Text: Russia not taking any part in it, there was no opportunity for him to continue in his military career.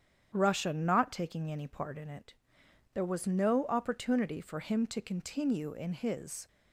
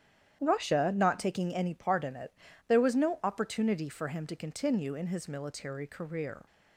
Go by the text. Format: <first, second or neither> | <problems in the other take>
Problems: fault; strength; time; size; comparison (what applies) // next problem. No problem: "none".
second | starts louder than the rest; strong; until 1.3 s; 9 dB; strong in the second // stops before "military career"; at 6.4 s